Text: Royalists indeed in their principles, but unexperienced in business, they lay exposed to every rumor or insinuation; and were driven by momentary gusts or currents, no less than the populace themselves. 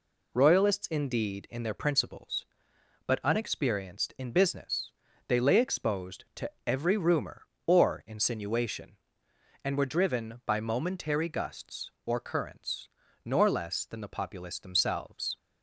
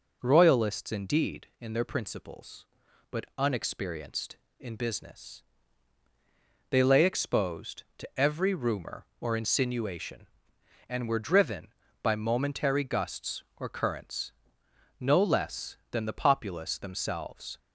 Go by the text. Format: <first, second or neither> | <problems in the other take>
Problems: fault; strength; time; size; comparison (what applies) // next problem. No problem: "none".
second | says "nor" for "no"; at 13.2 s